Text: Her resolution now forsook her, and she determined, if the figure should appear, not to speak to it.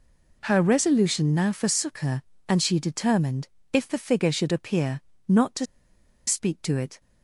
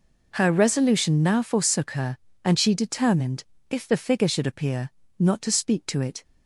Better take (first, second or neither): second